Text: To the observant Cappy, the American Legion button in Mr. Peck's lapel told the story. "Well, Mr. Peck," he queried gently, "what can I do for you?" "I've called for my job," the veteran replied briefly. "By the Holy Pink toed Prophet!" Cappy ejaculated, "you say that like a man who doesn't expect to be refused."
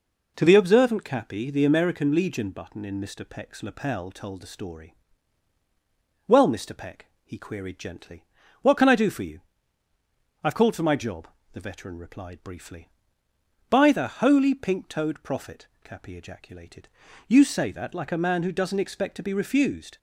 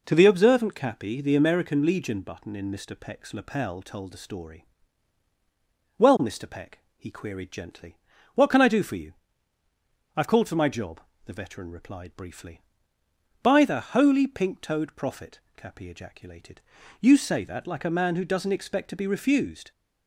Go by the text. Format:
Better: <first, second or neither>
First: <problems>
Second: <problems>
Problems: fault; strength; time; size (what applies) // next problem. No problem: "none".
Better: neither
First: none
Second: none